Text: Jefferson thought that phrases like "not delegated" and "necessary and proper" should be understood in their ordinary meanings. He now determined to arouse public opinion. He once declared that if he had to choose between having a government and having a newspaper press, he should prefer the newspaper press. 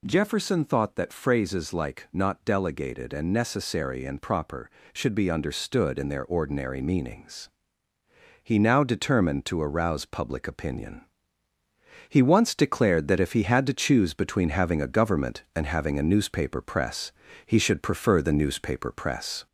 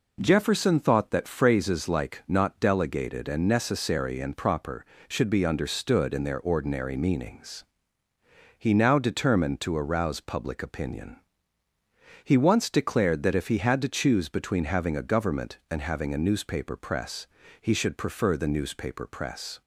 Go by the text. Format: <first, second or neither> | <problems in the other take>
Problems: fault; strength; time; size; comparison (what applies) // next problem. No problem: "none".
second | gets louder; slight; throughout; 2 dB